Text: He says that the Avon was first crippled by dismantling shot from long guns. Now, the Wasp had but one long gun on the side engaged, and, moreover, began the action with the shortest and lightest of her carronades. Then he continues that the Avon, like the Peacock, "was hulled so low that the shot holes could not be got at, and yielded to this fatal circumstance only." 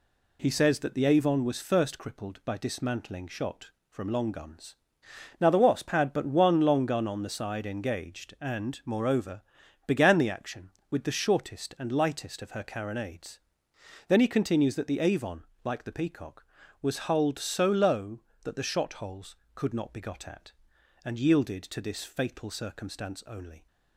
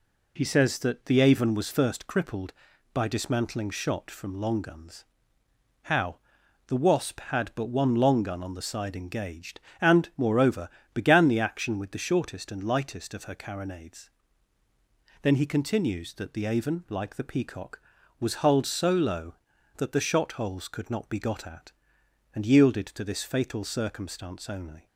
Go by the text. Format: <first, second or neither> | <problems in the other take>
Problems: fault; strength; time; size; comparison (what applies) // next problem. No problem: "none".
first | says "How" for "Now"; at 5.8 s